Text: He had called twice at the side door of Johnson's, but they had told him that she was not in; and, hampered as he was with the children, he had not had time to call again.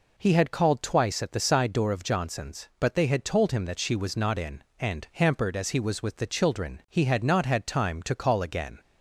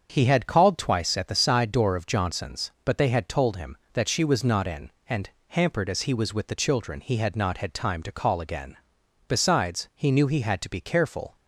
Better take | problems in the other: first | starts louder than the rest; until 1.1 s; 7 dB // goes on to say "Besides he knew he had to be careful"; strong; from 9.2 s on; 2.0 s long

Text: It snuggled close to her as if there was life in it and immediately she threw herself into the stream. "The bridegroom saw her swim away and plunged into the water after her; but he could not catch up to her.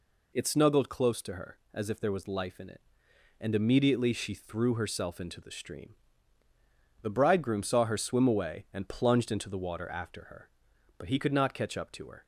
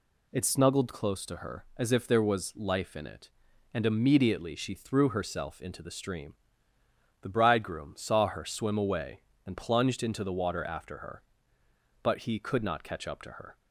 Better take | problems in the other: neither | none

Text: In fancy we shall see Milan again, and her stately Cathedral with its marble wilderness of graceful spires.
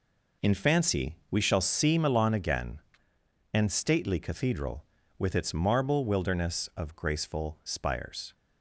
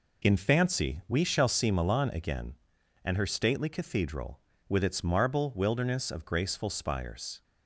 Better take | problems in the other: second | skips "her"; at 3.7 s

